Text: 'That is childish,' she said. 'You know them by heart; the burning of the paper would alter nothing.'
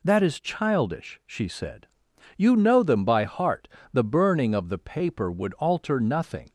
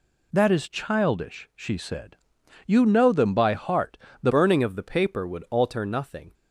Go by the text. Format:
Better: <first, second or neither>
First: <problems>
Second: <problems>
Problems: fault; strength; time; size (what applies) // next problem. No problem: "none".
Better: first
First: none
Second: changes voice at "burning"; from 4.2 s on; 2.1 s long